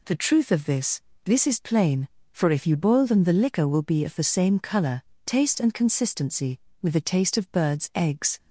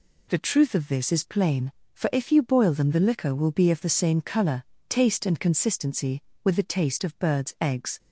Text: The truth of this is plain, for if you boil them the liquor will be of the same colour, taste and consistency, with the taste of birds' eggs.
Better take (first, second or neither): second